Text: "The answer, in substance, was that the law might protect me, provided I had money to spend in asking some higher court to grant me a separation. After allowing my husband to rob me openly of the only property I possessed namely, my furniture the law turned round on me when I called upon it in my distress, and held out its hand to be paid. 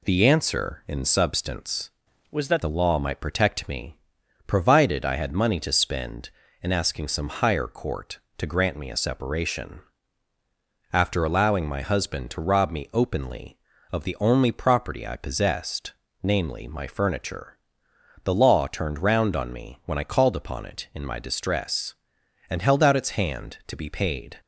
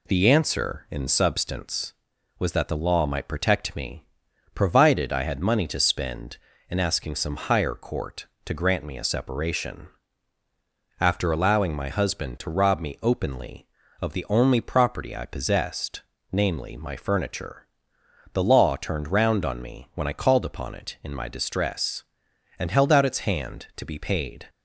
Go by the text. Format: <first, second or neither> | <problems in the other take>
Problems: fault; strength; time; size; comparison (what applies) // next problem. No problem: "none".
second | changes voice from "was" to "that"; from 2.2 to 2.6 s; 0.4 s long // pauses between "possessed" and "namely"; slight; at 15.9 s; 0.30 s long; slight in the second // pauses between "furniture" and "the"; noticeable; at 17.5 s; 0.66 s long; noticeable in the second